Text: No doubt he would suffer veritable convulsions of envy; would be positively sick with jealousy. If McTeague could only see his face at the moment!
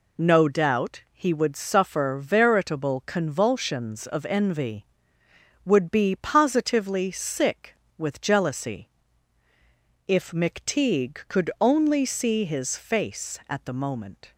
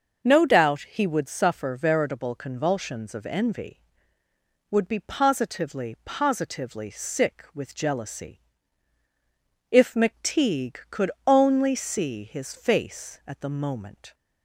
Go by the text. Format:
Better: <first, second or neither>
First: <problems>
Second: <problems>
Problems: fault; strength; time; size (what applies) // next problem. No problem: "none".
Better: first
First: none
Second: says "positively" twice; at 6.0 s // pauses between "could" and "only"; slight; at 11.0 s; 0.16 s long